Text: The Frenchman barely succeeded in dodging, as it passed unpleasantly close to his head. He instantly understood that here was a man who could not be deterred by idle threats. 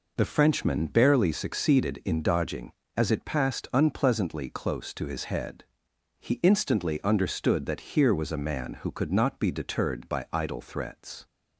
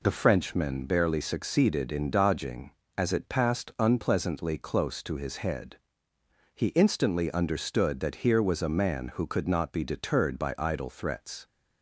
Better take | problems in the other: neither | none

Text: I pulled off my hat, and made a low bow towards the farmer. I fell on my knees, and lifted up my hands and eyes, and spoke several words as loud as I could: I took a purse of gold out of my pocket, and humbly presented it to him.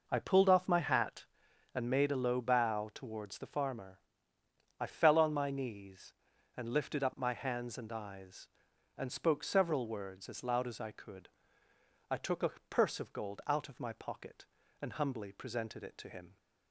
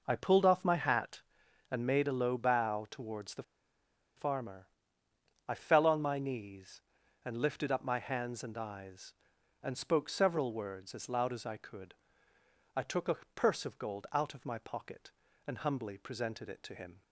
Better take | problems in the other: first | pauses between "the" and "farmer"; noticeable; at 3.4 s; 0.74 s long // pauses between "a" and "purse"; slight; at 13.1 s; 0.20 s long; slight in the first

